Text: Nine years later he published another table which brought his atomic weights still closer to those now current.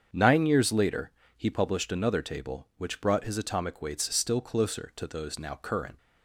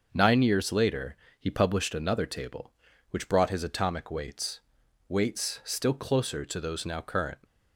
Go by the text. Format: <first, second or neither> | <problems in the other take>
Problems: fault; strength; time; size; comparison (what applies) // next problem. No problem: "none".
first | starts louder than the rest; noticeable; until 1.1 s; 6 dB; strong in the first // pauses between "later" and "he"; slight; at 1.1 s; 0.24 s long; slight in the first // says "weights" twice; at 5.0 s